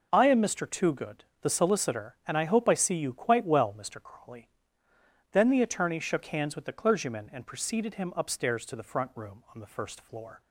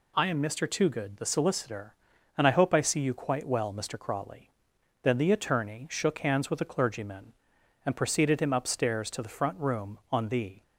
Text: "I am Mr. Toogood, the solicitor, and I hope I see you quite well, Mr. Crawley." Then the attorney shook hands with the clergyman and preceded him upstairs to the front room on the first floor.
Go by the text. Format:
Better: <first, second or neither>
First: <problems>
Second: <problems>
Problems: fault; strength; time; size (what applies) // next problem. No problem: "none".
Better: first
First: none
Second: stops before "first floor"; at 10.6 s